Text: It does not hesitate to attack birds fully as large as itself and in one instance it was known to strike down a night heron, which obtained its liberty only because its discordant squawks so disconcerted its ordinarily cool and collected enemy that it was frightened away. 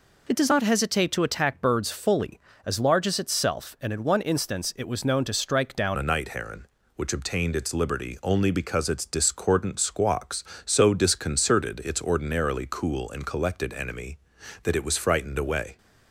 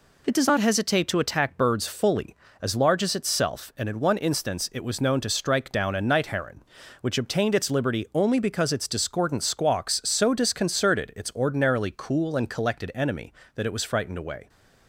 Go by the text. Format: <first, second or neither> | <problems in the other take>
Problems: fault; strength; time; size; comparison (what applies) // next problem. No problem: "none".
second | changes voice at "a"; from 5.9 s on; 9.8 s long